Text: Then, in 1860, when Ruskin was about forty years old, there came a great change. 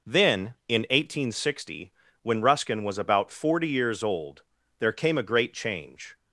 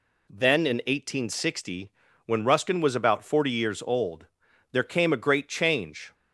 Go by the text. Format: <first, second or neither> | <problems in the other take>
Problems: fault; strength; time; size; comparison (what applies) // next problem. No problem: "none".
neither | none